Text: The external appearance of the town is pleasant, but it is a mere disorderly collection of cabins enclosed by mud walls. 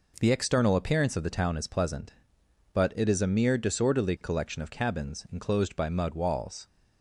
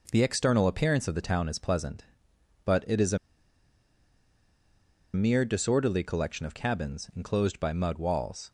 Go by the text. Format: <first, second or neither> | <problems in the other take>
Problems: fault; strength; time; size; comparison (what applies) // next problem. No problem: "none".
first | pauses between "a" and "mere"; strong; at 3.1 s; 1.9 s long